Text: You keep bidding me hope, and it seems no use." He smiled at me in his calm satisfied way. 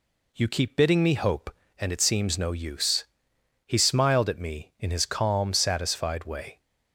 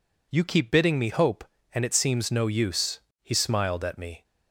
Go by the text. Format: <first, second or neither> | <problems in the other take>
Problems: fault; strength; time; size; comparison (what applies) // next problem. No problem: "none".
first | stops before "in his calm satisfied way"; at 4.2 s